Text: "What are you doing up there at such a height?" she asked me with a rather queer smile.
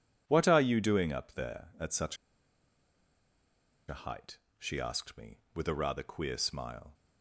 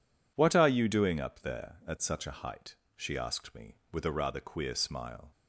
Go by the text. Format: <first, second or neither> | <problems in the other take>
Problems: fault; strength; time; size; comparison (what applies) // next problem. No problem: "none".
second | pauses between "such" and "a"; strong; at 2.1 s; 1.7 s long